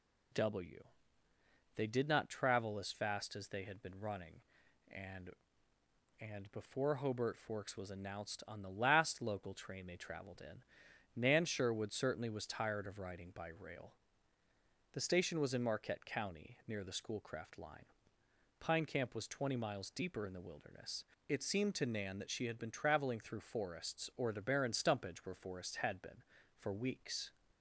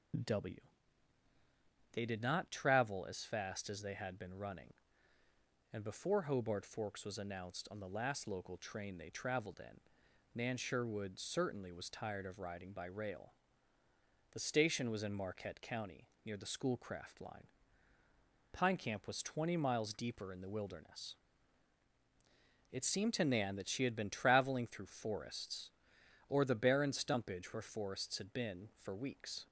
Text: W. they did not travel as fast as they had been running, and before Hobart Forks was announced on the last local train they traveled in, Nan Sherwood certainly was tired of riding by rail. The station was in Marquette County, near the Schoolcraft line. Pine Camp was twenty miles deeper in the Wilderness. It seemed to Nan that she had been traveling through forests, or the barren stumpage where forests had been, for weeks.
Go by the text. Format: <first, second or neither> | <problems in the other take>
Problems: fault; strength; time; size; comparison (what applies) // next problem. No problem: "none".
second | says "and" twice; at 6.1 s